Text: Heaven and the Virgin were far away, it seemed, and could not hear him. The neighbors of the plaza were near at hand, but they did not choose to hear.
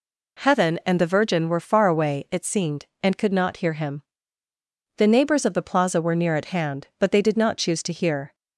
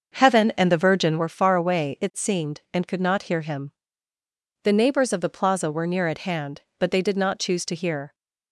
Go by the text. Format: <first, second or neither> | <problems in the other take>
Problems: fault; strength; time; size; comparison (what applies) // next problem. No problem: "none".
first | starts louder than the rest; until 1.3 s; 6.5 dB